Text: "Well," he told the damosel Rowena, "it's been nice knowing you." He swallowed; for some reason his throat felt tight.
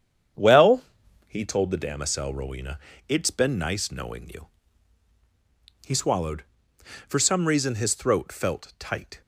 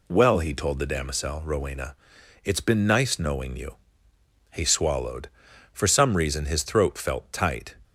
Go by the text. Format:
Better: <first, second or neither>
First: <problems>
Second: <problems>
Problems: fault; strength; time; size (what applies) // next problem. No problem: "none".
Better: second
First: starts louder than the rest; strong; until 1.4 s; 8.5 dB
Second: none